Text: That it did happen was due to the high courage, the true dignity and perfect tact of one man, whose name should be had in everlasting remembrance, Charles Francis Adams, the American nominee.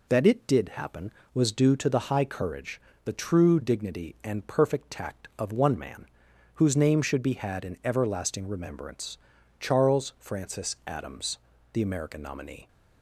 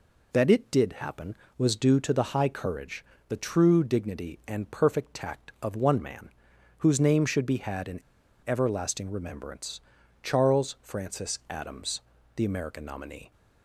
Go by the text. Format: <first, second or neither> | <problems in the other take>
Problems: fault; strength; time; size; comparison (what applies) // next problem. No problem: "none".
first | pauses between "in" and "everlasting"; at 8.0 s; 0.45 s long